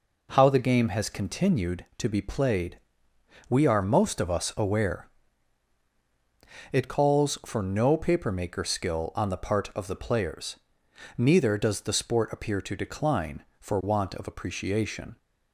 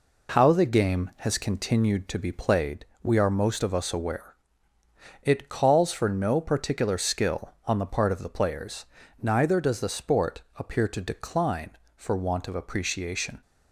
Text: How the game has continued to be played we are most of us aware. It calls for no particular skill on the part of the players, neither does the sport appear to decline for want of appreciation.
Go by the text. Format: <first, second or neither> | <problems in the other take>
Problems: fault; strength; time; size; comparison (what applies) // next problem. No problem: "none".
second | pauses between "played" and "we"; noticeable; at 2.7 s; 0.72 s long; slight in the second // says "papermaker" for "particular"; at 7.9 s